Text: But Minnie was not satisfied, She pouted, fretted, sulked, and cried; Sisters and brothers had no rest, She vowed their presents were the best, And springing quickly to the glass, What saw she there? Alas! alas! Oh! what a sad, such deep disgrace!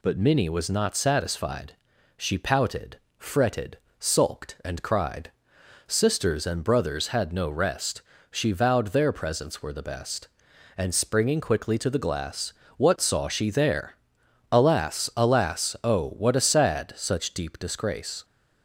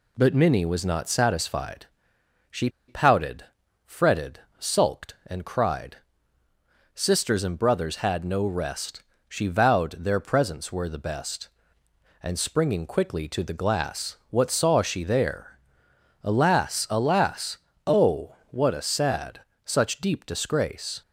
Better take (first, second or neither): first